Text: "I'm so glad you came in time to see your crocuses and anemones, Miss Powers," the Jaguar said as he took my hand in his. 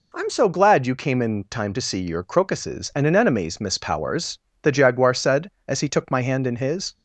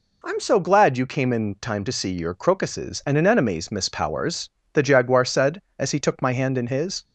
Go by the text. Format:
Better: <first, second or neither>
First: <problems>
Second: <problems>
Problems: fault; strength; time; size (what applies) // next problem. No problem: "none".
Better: neither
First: none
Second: none